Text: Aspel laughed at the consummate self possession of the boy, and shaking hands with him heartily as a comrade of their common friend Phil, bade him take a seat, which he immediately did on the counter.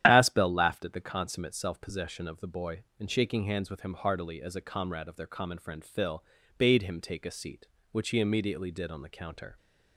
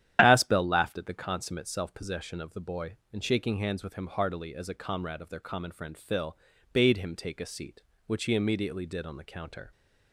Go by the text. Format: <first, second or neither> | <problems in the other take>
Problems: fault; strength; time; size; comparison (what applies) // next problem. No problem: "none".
neither | starts louder than the rest; strong; the same in both